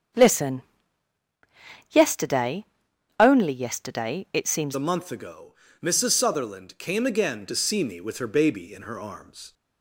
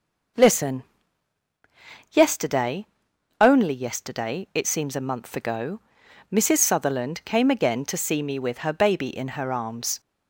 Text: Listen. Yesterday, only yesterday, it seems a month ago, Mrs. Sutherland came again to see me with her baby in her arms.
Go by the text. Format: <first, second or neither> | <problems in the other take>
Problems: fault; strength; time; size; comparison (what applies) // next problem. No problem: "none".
second | starts louder than the rest; strong; until 2.4 s; 7 dB // changes voice at "a"; from 4.7 s on; 4.8 s long